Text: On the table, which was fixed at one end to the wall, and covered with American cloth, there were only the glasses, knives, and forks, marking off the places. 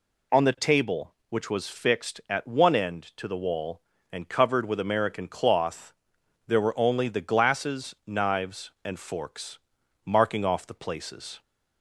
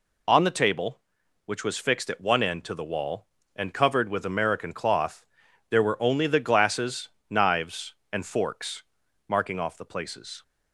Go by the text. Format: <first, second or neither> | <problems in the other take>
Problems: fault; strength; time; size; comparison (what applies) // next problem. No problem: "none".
neither | none